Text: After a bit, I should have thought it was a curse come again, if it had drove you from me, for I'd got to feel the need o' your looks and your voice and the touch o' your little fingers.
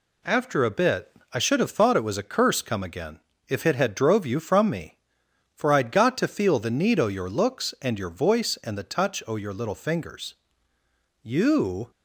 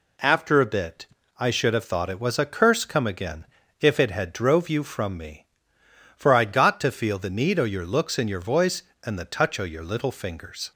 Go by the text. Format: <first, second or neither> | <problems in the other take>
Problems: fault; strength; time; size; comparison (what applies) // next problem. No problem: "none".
second | goes on to say "You"; noticeable; from 11.2 s on; 0.68 s long